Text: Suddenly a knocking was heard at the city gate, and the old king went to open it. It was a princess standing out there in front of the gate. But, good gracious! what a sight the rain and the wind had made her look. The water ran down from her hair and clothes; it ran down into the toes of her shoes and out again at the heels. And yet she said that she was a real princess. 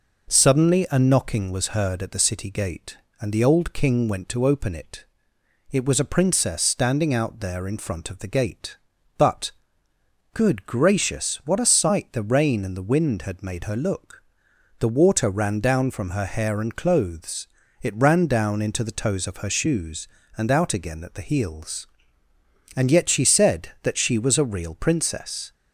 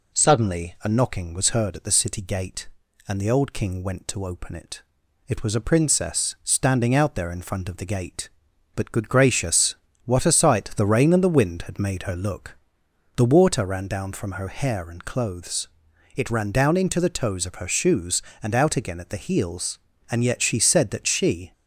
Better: first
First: none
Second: stops before "was a real princess"; at 21.5 s

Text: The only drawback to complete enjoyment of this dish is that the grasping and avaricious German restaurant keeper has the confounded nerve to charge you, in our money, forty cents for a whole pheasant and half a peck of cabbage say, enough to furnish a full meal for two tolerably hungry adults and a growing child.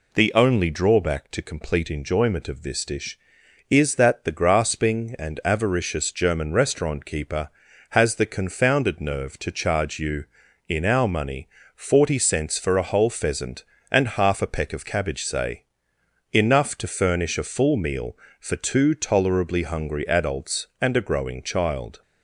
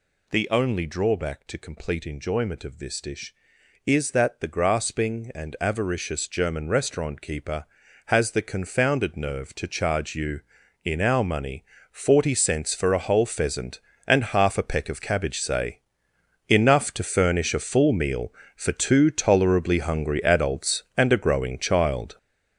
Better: first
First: none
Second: gets louder; strong; throughout; 8.5 dB

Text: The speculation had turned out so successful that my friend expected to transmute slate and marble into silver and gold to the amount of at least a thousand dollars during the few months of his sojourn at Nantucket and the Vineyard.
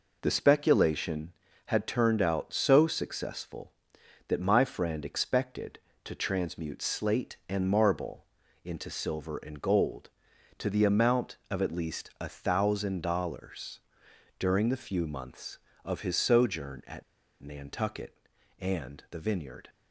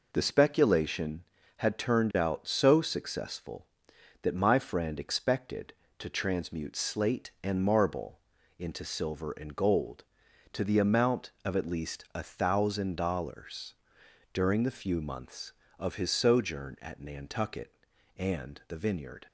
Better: second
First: pauses between "marble" and "into"; slight; at 8.2 s; 0.36 s long // pauses between "dollars" and "during"; noticeable; at 13.8 s; 0.58 s long // pauses between "at" and "Nantucket"; at 17.0 s; 0.39 s long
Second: pauses between "marble" and "into"; slight; at 8.2 s; 0.36 s long // pauses between "dollars" and "during"; noticeable; at 13.7 s; 0.58 s long

